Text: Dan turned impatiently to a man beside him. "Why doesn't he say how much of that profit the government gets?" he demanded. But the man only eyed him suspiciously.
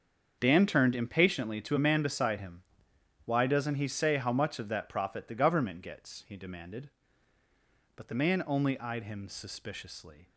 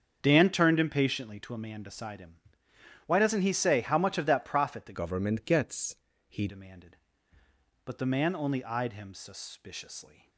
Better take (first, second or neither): first